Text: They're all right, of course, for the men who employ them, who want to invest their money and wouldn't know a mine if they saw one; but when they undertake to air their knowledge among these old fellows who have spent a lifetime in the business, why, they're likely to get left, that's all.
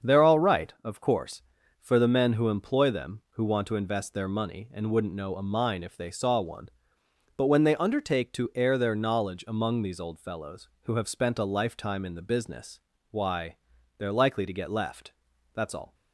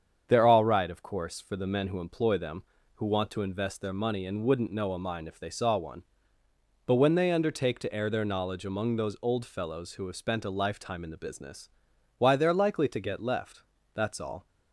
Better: first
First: starts louder than the rest; strong; until 1.1 s; 7.5 dB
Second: starts louder than the rest; strong; until 1.2 s; 7.5 dB // says "those" for "these"; at 8.9 s

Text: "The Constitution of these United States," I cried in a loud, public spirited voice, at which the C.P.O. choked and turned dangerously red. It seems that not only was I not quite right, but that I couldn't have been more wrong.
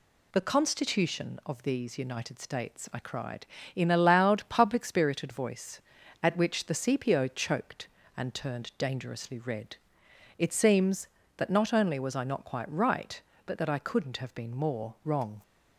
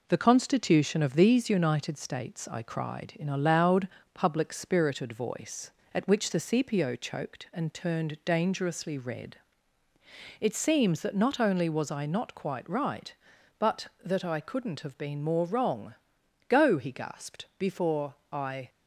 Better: first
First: none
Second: goes on to say "Go he gasped before I"; strong; from 16.4 s on; 2.2 s long

